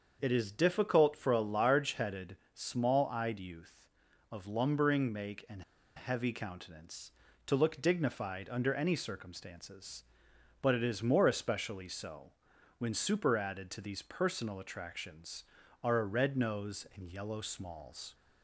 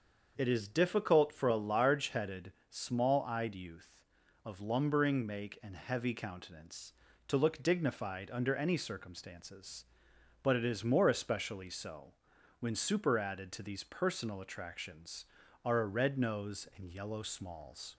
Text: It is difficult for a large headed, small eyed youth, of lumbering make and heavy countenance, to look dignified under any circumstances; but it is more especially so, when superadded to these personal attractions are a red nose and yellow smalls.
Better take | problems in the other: second | starts louder than the rest; until 1.2 s; 6.5 dB; also in the second // pauses between "and" and "heavy"; slight; at 5.6 s; 0.34 s long

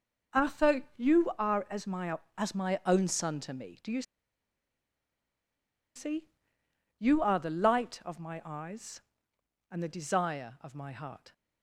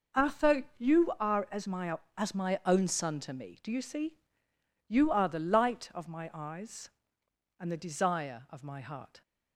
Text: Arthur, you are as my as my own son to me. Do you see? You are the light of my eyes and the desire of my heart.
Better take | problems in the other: second | pauses between "you" and "see"; strong; at 4.0 s; 1.9 s long

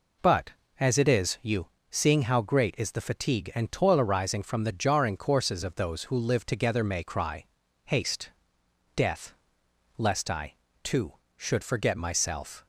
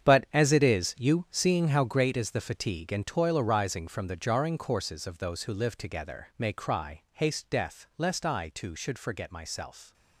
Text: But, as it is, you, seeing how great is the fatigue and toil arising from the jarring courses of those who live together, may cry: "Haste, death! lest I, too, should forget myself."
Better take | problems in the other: first | gets quieter; strong; throughout; 11.5 dB

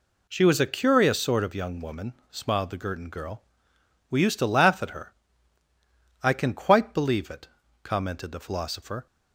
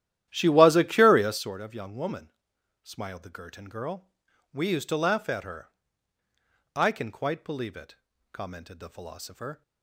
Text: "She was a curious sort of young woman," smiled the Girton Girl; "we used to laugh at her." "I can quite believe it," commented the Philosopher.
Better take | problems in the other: first | starts louder than the rest; strong; until 1.6 s; 12 dB

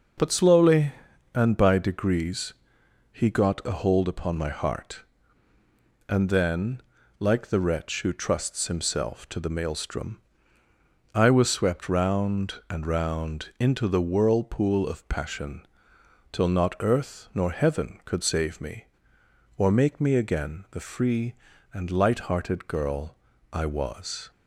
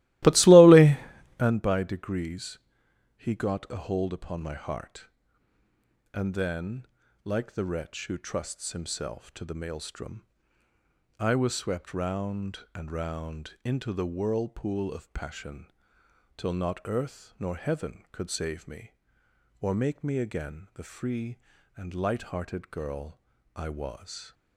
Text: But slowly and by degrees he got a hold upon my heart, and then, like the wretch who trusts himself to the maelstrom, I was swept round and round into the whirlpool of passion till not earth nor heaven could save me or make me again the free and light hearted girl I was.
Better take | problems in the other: first | starts louder than the rest; strong; until 1.6 s; 17 dB // pauses between "degrees" and "he"; noticeable; at 2.5 s; 0.60 s long; noticeable in the first // pauses between "passion" and "till"; noticeable; at 15.6 s; 0.68 s long; noticeable in the first // pauses between "girl" and "I"; slight; at 23.1 s; 0.36 s long; slight in the first

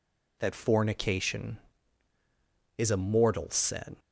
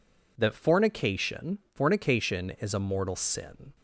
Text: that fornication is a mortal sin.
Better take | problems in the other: first | says "fornication" twice; at 1.7 s

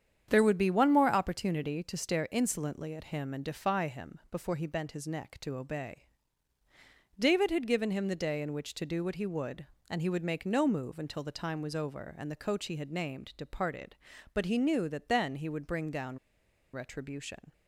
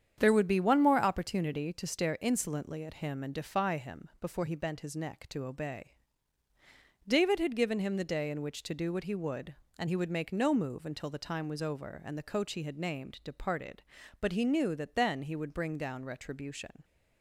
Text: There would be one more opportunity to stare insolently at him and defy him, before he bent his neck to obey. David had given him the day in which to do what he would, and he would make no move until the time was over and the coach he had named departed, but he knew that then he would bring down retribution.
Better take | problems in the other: second | starts louder than the rest; strong; until 1.3 s; 8.5 dB; strong in the second // pauses between "down" and "retribution"; noticeable; at 16.1 s; 0.55 s long

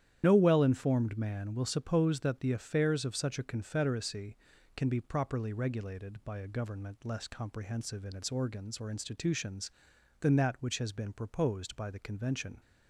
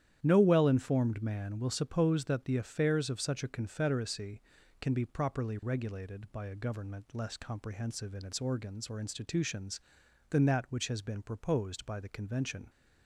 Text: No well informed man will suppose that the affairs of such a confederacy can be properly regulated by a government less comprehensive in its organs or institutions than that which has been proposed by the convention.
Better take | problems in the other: second | loses the start of "No"; at 0.2 s; 60 ms // starts louder than the rest; strong; until 1.2 s; 10.5 dB; strong in the second

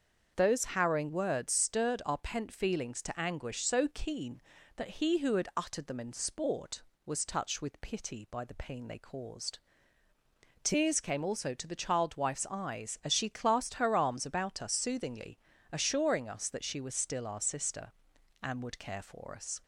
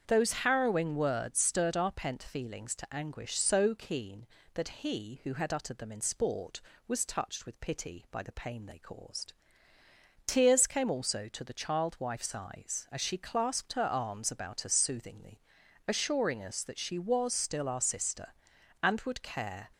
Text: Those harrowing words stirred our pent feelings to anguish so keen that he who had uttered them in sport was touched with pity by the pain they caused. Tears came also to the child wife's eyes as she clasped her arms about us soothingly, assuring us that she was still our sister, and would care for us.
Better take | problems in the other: first | starts louder than the rest; strong; until 1.0 s; 7 dB; also in the first // stops before "for us"; at 19.7 s

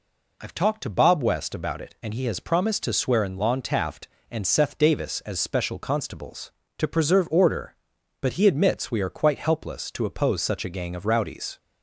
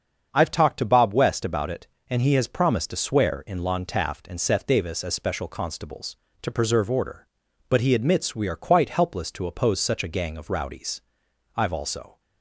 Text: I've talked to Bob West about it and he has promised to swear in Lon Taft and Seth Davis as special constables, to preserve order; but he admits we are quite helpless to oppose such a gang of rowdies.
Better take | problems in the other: first | starts louder than the rest; until 1.3 s; 7 dB // goes on to say "I've also"; noticeable; from 11.5 s on; 0.64 s long

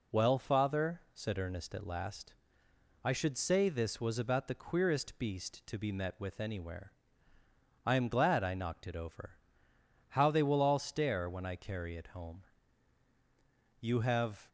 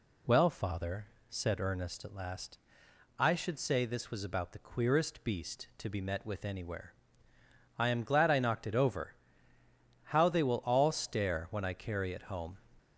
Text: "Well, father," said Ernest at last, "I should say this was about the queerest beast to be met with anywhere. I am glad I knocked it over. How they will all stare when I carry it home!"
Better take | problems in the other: second | goes on to say "You have"; noticeable; from 13.8 s on; 0.68 s long

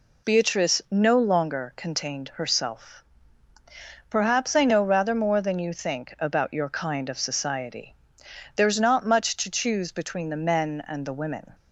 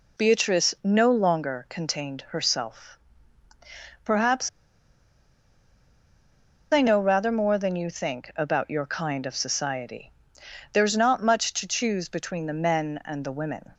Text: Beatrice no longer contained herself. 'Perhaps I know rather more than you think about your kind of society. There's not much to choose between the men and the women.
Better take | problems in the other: first | pauses between "Perhaps" and "I"; strong; at 4.4 s; 2.2 s long

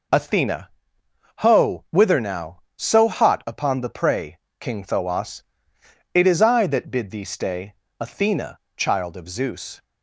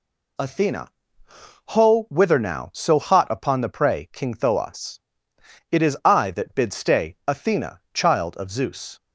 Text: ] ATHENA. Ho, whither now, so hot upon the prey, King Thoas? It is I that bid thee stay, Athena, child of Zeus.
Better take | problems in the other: first | skips "thee"; at 6.7 s

